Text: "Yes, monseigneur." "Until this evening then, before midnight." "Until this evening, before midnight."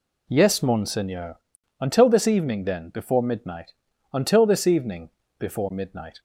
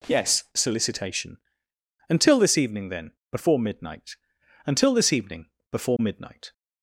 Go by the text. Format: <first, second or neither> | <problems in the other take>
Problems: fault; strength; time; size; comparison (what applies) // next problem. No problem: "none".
first | says "solicitation" for "monseigneur"; at 0.5 s